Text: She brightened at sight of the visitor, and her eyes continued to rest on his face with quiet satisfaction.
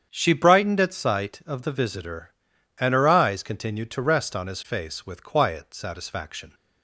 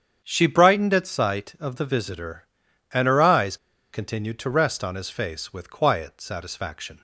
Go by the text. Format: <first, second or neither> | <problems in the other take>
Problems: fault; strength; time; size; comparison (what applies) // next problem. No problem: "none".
first | starts louder than the rest; strong; until 1.2 s; 8 dB; strong in the first // pauses between "eyes" and "continued"; at 3.5 s; 0.36 s long